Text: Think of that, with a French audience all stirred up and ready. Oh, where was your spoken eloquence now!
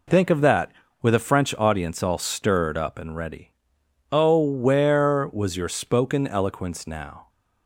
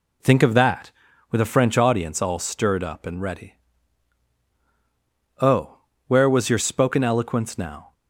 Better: neither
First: none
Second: none

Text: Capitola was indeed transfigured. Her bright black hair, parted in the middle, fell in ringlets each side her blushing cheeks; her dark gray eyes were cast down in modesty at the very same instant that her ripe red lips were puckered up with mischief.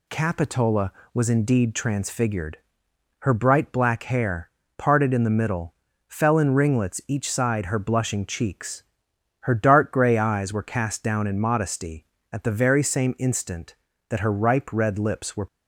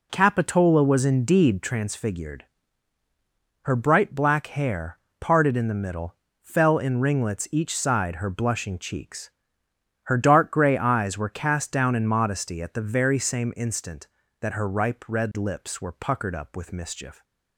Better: second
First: stops before "puckered up with mischief"; at 15.4 s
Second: none

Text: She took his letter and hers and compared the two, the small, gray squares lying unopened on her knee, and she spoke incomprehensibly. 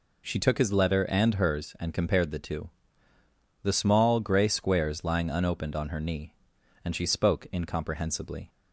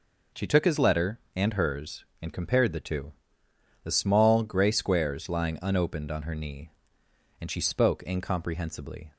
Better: neither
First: none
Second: none

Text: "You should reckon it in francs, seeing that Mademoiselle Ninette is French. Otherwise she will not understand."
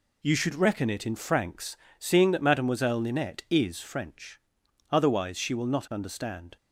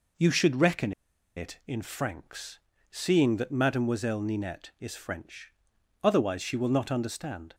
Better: first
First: none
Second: pauses between "reckon" and "it"; at 0.9 s; 0.44 s long

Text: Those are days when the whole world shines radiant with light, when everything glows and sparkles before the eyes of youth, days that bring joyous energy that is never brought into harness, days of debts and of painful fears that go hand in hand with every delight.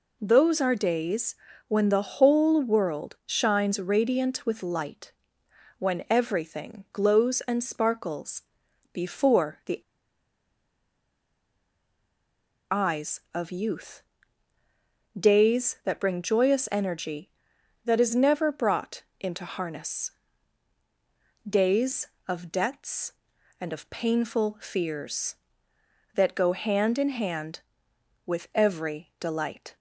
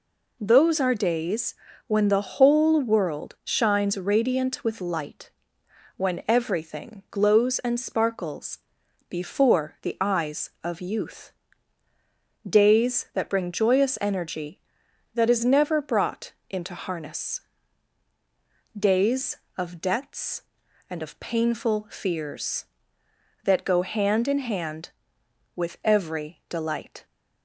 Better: second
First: pauses between "days" and "when"; slight; at 1.3 s; 0.34 s long // pauses between "sparkles" and "before"; noticeable; at 8.4 s; 0.54 s long // pauses between "the" and "eyes"; strong; at 9.7 s; 2.9 s long // pauses between "brought" and "into"; slight; at 19.0 s; 0.18 s long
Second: pauses between "days" and "when"; slight; at 1.5 s; 0.34 s long // pauses between "sparkles" and "before"; noticeable; at 8.5 s; 0.54 s long // pauses between "brought" and "into"; slight; at 16.3 s; 0.18 s long

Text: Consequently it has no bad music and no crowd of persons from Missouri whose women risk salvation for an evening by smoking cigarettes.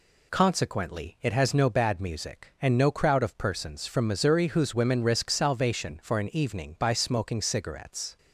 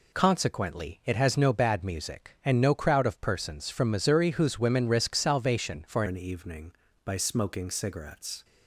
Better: first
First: none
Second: changes voice at "an"; from 6.0 s on; 2.4 s long

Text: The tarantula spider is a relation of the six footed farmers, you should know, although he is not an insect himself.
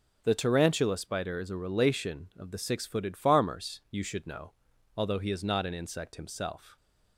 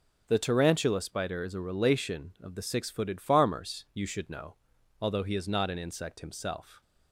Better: neither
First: none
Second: none

